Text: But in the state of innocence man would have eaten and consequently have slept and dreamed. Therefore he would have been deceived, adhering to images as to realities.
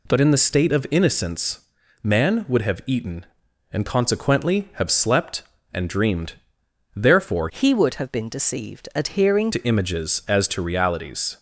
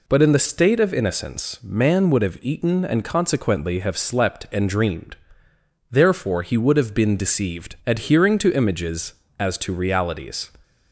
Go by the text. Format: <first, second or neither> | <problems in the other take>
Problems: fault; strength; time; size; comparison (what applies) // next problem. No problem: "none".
second | pauses between "innocence" and "man"; at 1.6 s; 0.42 s long // changes voice from "he" to "adhering"; from 7.4 to 9.5 s; 2.1 s long